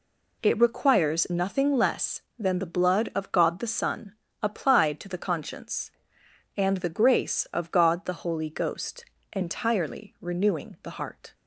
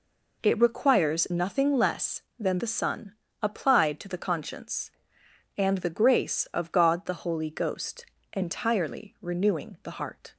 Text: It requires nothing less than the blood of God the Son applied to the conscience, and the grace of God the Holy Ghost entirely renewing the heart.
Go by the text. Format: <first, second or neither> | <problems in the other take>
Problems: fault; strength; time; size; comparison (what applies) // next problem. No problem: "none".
first | skips "the blood of God"; at 2.5 s // pauses between "Son" and "applied"; slight; at 3.1 s; 0.26 s long; slight in the first // pauses between "Ghost" and "entirely"; slight; at 8.0 s; 0.28 s long; slight in the first